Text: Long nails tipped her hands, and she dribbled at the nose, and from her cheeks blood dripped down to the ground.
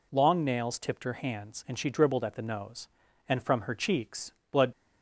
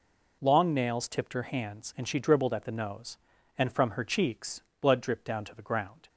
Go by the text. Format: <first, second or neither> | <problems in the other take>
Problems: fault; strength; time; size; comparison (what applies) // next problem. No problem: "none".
second | pauses between "cheeks" and "blood"; slight; at 4.3 s; 0.20 s long; slight in the second // stops before "dripped down to the ground"; at 4.7 s